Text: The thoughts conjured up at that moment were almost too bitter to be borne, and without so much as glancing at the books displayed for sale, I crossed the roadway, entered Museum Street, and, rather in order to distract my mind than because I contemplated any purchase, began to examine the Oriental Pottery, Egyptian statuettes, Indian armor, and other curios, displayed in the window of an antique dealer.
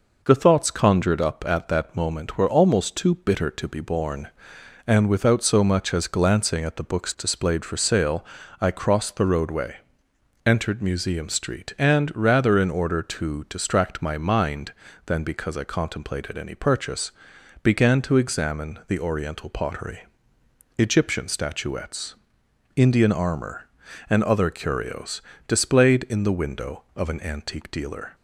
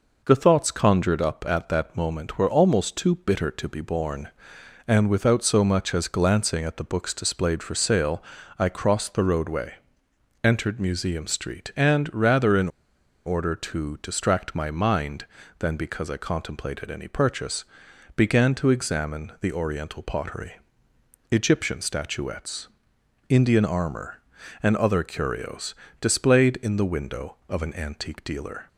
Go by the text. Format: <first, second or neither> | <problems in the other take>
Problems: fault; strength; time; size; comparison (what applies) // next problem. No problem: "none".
first | pauses between "in" and "order"; noticeable; at 12.6 s; 0.57 s long